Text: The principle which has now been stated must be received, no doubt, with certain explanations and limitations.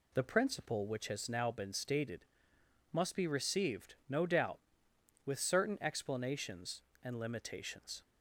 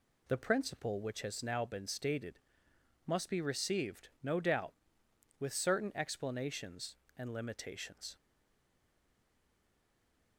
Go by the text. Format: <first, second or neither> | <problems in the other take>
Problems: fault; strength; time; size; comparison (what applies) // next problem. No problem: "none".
first | pauses between "stated" and "must"; noticeable; at 2.3 s; 0.68 s long; noticeable in the first // stays silent after the last word; from 8.1 s on; 2.2 s long